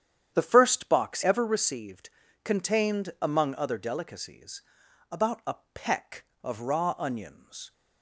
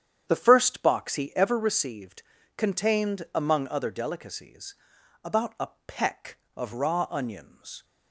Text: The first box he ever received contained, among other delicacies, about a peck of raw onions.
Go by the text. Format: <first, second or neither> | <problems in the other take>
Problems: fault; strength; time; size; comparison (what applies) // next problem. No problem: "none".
second | starts louder than the rest; strong; until 1.3 s; 9 dB; strong in the second // skips "he"; at 1.2 s // pauses between "received" and "contained"; slight; at 2.0 s; 0.36 s long; slight in the second // pauses between "a" and "peck"; slight; at 5.5 s; 0.18 s long; slight in the second